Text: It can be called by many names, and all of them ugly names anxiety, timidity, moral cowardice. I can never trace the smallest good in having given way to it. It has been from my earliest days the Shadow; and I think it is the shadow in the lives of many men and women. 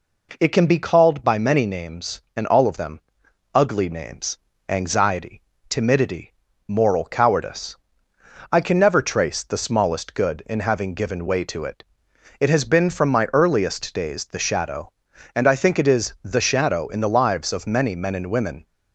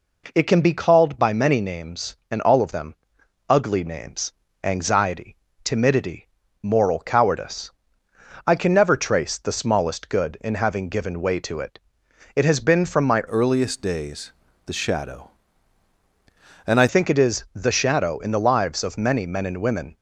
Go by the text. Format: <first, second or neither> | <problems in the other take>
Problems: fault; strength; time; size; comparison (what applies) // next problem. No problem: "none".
first | pauses between "them" and "ugly"; noticeable; at 2.9 s; 0.52 s long; noticeable in the first // pauses between "names" and "anxiety"; slight; at 4.3 s; 0.30 s long; slight in the first // changes voice from "earliest" to "I"; from 13.2 to 16.8 s; 3.6 s long // pauses between "days" and "the"; slight; at 14.3 s; 0.36 s long